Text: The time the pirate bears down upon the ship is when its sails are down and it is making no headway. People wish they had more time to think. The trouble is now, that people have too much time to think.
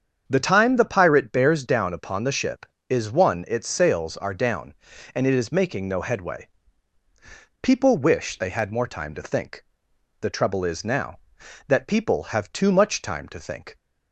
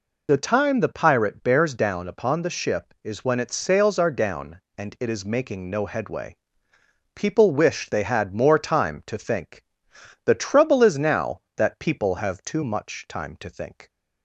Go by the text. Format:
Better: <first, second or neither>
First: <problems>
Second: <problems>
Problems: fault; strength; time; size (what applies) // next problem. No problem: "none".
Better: second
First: starts louder than the rest; strong; until 1.3 s; 7.5 dB // says "one" for "when"; at 3.1 s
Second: none